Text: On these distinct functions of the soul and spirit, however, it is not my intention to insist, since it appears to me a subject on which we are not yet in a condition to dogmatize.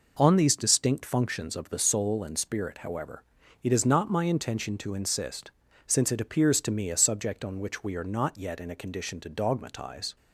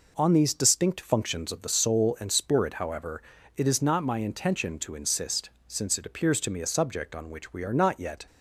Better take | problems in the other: first | stops before "in a condition to dogmatize"; at 8.2 s

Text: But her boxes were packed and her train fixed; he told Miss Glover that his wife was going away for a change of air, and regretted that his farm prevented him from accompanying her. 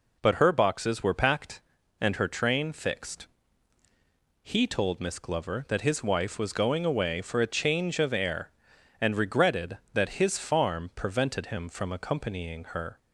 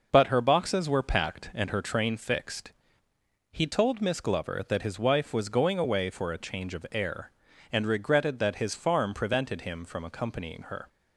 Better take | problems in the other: neither | none

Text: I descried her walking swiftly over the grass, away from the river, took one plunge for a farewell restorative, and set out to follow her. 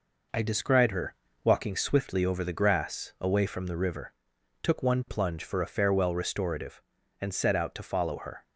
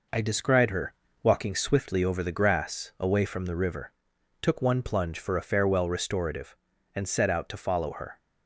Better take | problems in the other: neither | pauses between "her" and "walking"; slight; the same in both

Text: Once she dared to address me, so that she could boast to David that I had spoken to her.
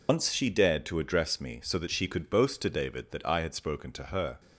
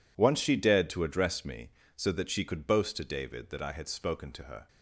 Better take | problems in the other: second | loses the start of "Once"; at 0.0 s; 105 ms

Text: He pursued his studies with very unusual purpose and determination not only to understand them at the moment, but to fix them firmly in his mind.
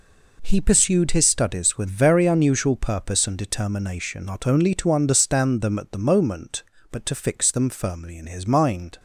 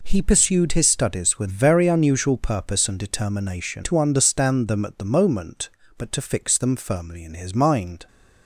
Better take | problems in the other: first | skips "not only"; at 3.8 s

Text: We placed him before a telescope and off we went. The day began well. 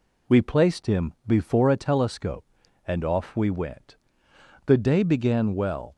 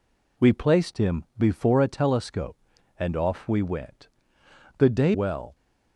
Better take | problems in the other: first | pauses between "him" and "before"; slight; at 1.2 s; 0.16 s long; slight in the first // skips "began"; at 5.1 s

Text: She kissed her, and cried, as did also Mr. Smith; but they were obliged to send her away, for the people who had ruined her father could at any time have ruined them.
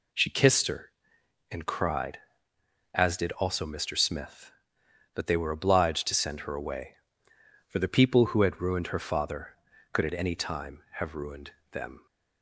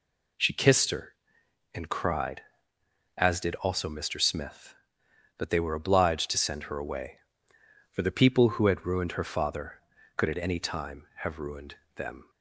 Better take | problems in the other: neither | pauses between "ruined" and "them"; slight; the same in both

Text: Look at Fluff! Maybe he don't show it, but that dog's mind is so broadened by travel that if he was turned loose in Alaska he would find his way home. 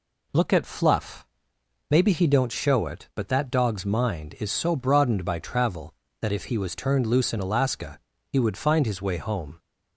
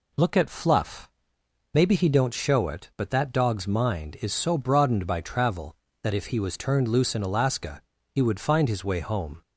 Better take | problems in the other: neither | pauses between "Alaska" and "he"; slight; the same in both

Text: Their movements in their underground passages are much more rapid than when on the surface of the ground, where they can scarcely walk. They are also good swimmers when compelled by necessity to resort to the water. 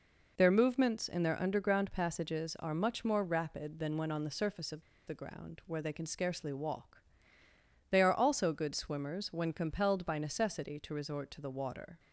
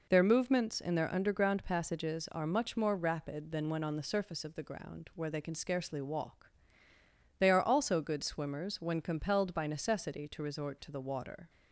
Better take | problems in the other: second | pauses between "of" and "the"; slight; at 4.8 s; 0.25 s long

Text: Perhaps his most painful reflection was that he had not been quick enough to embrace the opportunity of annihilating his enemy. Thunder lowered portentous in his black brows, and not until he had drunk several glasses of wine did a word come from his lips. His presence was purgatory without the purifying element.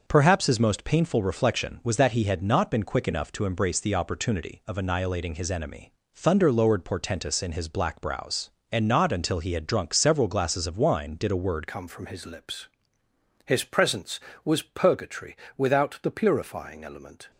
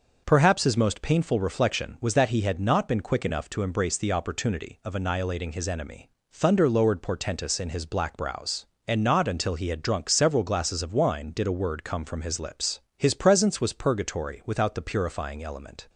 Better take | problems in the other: second | changes voice at "come"; from 11.6 s on; 5.7 s long // pauses between "purgatory" and "without"; slight; at 15.3 s; 0.22 s long

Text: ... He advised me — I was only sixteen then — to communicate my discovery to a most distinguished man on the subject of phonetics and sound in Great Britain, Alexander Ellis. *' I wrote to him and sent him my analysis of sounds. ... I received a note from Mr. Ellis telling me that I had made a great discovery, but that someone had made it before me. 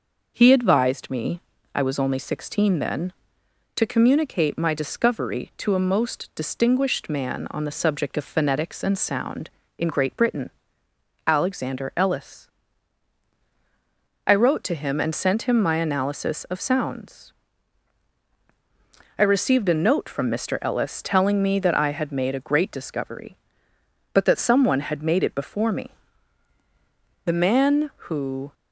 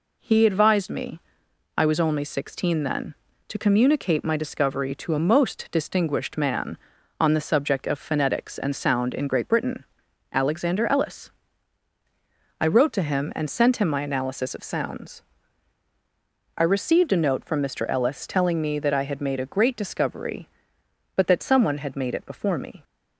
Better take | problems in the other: second | goes on to say "The man who"; noticeable; from 27.2 s on; 1.3 s long

